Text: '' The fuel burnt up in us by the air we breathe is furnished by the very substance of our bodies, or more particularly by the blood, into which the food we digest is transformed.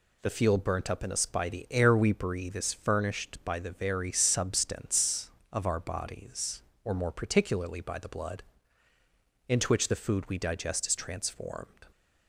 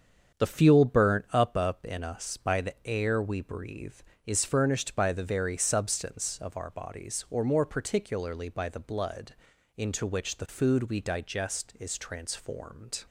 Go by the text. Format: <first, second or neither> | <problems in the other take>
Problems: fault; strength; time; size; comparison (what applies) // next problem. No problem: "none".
first | starts louder than the rest; strong; until 1.4 s; 7.5 dB // says "up" twice; at 1.5 s